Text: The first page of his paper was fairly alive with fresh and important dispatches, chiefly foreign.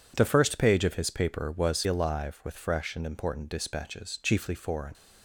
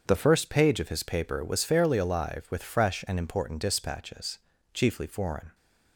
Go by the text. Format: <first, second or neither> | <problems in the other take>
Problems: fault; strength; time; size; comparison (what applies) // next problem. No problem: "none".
second | skips "fairly"; at 1.8 s